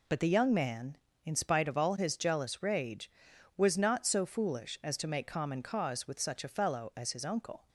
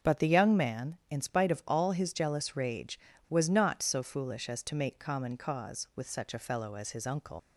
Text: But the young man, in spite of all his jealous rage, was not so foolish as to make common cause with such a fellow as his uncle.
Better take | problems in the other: first | starts louder than the rest; until 1.1 s; 6.5 dB // leaves "uncle" unfinished; at 7.3 s; 105 ms

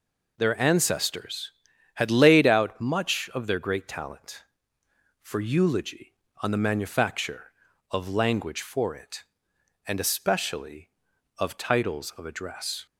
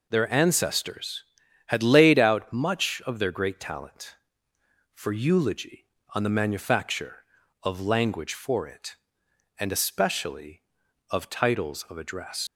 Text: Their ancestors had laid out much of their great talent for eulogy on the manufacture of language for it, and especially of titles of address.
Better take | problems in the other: first | leaves "address" unfinished; at 12.4 s; 105 ms

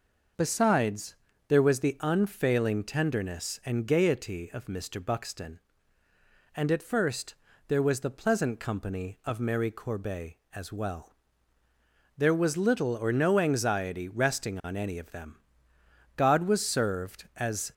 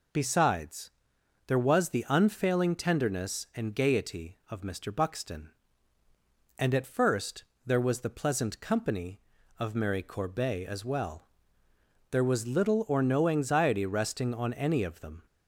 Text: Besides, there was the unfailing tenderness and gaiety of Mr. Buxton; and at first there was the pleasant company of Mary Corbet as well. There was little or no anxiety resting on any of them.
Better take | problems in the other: second | pauses between "first" and "there"; slight; at 7.3 s; 0.32 s long; slight in the second // goes on to say "God was served as"; from 16.1 s on; 1.5 s long

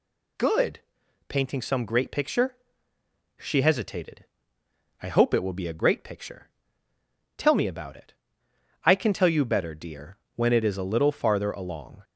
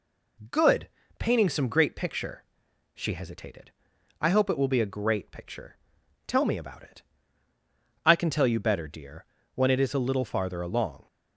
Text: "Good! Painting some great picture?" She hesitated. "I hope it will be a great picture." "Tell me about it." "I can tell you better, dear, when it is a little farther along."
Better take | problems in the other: neither | none

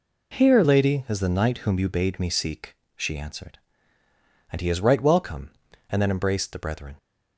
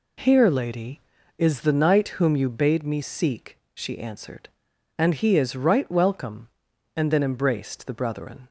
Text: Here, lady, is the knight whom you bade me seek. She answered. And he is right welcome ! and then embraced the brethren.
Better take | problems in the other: second | changes voice at "lady"; from 0.6 s on; 6.3 s long

